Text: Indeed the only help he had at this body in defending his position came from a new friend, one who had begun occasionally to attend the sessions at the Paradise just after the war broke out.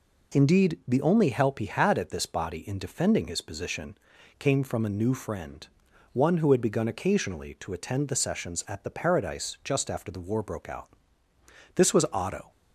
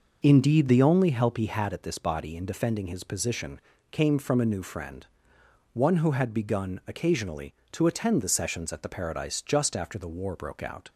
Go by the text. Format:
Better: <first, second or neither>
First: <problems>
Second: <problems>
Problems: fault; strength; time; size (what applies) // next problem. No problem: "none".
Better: second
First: pauses between "position" and "came"; at 3.9 s; 0.42 s long // goes on to say "This was Otto"; noticeable; from 11.7 s on; 0.76 s long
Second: pauses between "position" and "came"; slight; at 3.6 s; 0.30 s long